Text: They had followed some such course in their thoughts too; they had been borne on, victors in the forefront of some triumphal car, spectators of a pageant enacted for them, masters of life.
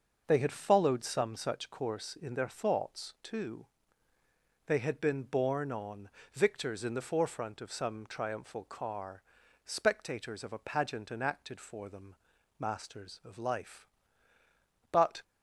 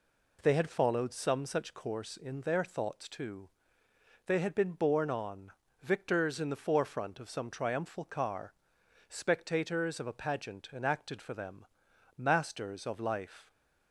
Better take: second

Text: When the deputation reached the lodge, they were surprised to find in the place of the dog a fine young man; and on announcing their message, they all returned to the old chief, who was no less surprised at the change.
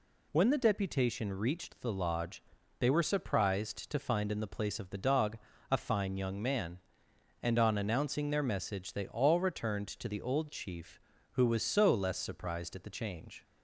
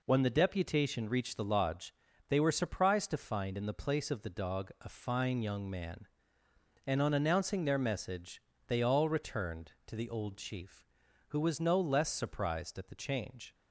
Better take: second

